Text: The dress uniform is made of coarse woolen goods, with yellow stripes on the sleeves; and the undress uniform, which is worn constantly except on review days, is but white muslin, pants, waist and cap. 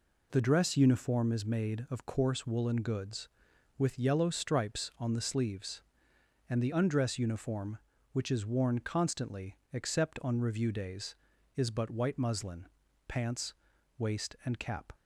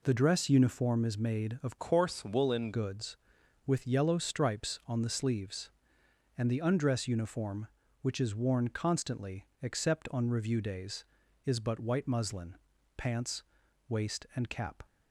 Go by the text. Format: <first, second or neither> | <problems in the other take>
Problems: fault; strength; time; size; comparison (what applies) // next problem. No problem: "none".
first | changes voice from "coarse" to "woolen"; from 1.7 to 2.7 s; 1.0 s long // pauses between "constantly" and "except"; slight; at 9.4 s; 0.16 s long; slight in the first